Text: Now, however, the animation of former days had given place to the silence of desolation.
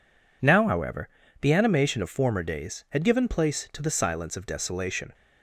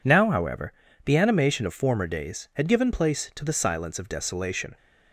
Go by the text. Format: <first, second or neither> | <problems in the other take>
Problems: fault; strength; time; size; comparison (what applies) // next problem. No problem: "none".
neither | none